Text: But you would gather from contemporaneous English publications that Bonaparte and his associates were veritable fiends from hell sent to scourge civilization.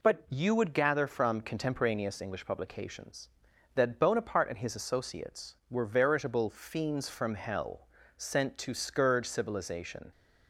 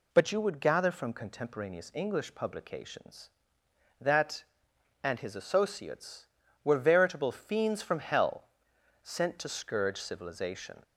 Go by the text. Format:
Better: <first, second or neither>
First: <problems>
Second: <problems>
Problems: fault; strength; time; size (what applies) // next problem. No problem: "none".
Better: first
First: pauses between "hell" and "sent"; slight; at 7.8 s; 0.30 s long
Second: skips "Bonaparte"; at 4.7 s // pauses between "hell" and "sent"; noticeable; at 8.4 s; 0.58 s long